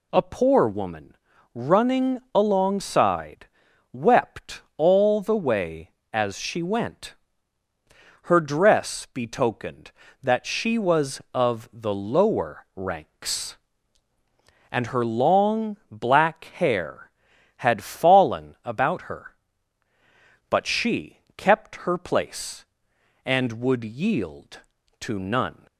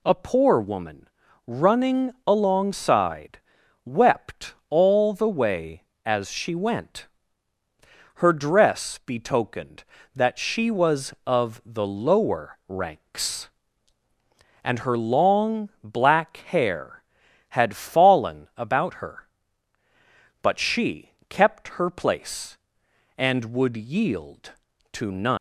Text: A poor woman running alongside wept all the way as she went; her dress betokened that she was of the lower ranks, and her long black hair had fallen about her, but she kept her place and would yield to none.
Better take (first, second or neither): first